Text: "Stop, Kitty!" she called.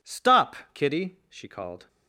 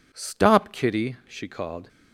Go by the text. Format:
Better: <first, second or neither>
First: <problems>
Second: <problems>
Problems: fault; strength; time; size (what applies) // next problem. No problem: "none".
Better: neither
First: none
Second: none